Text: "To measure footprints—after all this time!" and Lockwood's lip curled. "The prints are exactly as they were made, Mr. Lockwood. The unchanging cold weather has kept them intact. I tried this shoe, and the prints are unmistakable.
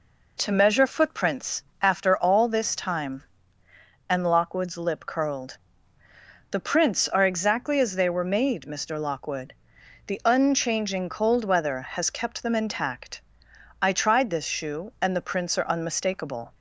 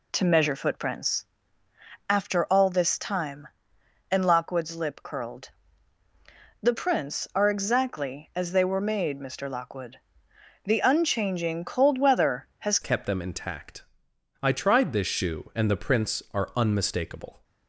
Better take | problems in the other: first | changes voice at "kept"; from 12.8 s on; 4.6 s long

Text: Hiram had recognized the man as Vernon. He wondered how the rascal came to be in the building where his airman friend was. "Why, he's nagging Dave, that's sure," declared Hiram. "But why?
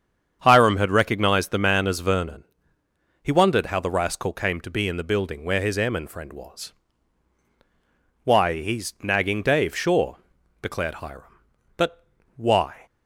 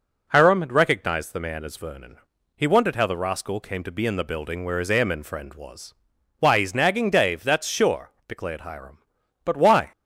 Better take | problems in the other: second | starts louder than the rest; strong; until 1.4 s; 8 dB // skips "that's"; at 9.7 s // pauses between "But" and "why"; slight; at 12.0 s; 0.32 s long

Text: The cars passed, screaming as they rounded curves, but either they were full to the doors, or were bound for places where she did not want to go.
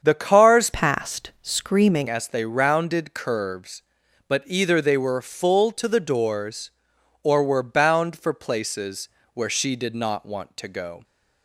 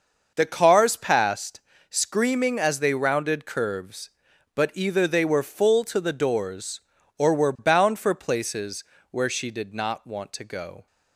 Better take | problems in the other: second | starts louder than the rest; strong; until 1.0 s; 7.5 dB; also in the second // changes voice from "passed" to "screaming"; from 0.7 to 2.0 s; 1.3 s long // pauses between "places" and "where"; slight; at 9.0 s; 0.24 s long; slight in the second

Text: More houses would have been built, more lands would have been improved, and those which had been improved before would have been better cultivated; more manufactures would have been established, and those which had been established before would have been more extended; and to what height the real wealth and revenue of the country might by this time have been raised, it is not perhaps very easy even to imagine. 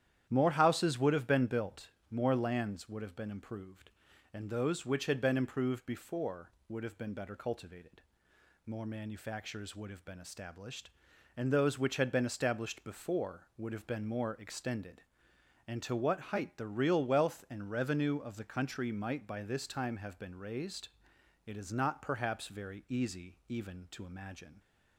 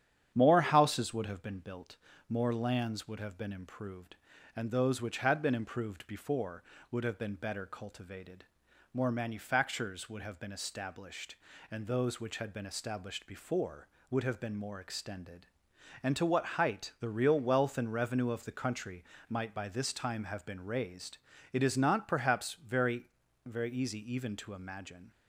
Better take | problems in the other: first | starts louder than the rest; strong; until 1.3 s; 9 dB; strong in the first // pauses between "country" and "might"; slight; at 19.0 s; 0.26 s long // says "very" twice; at 23.4 s // pauses between "easy" and "even"; slight; at 23.9 s; 0.16 s long

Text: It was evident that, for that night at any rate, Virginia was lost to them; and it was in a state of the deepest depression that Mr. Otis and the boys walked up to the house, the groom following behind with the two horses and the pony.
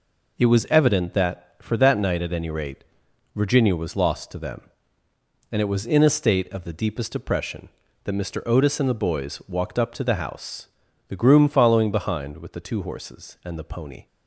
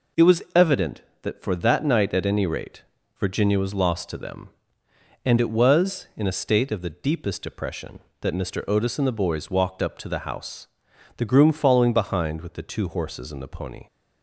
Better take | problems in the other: neither | none

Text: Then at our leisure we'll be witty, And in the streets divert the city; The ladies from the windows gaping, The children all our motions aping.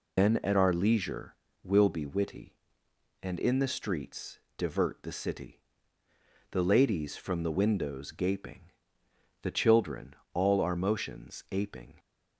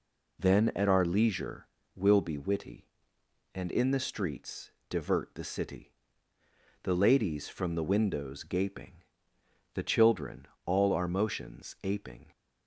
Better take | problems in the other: second | loses the start of "Then"; at 0.1 s; 105 ms // pauses between "leisure" and "we'll"; slight; at 1.3 s; 0.28 s long; slight in the second // pauses between "streets" and "divert"; slight; at 4.3 s; 0.18 s long; slight in the second // pauses between "children" and "all"; slight; at 10.1 s; 0.18 s long; slight in the second

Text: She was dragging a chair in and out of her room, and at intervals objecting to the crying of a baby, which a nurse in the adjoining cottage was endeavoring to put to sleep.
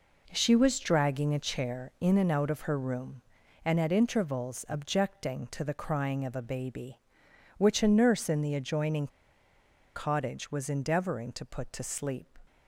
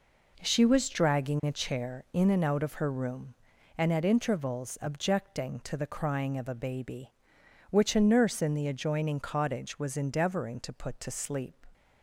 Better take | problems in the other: second | pauses between "adjoining" and "cottage"; noticeable; at 9.0 s; 0.88 s long

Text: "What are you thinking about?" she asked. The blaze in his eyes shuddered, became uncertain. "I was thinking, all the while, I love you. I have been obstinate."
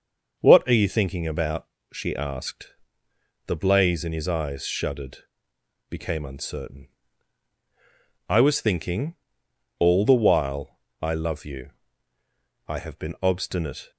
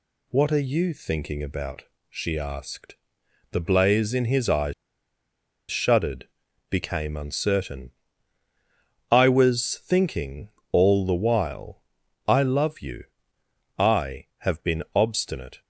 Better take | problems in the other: first | pauses between "eyes" and "shuddered"; noticeable; at 4.7 s; 0.97 s long

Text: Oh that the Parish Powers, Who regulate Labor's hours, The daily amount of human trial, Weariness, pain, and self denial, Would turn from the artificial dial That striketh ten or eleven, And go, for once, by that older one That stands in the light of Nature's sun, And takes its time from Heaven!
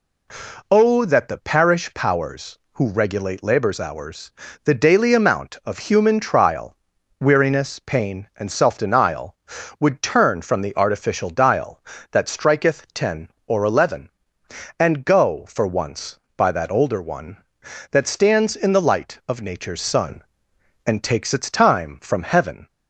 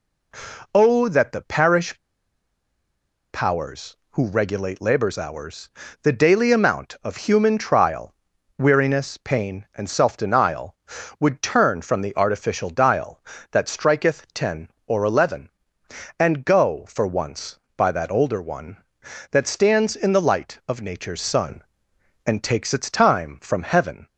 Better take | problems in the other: first | pauses between "Parish" and "Powers"; strong; at 1.9 s; 1.3 s long

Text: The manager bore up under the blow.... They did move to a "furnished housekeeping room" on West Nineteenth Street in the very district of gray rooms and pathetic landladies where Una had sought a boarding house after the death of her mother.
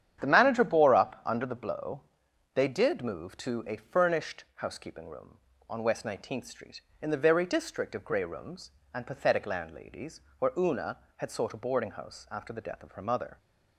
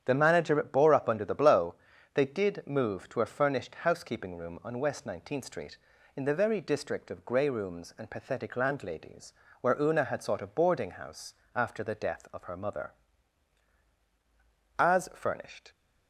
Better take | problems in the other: first | starts louder than the rest; strong; until 1.0 s; 9 dB; strong in the first // pauses between "landladies" and "where"; slight; at 9.3 s; 0.28 s long; slight in the first // pauses between "house" and "after"; slight; at 11.3 s; 0.20 s long // goes on to say "As furnished"; noticeable; from 14.7 s on; 0.94 s long

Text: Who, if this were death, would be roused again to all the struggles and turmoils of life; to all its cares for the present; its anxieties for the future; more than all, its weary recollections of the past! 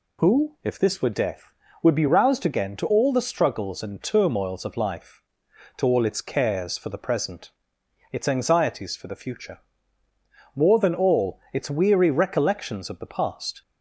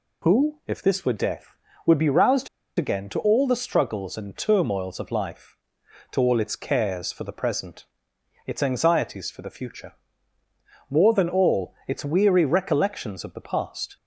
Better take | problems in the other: first | pauses between "roused" and "again"; slight; at 2.4 s; 0.29 s long

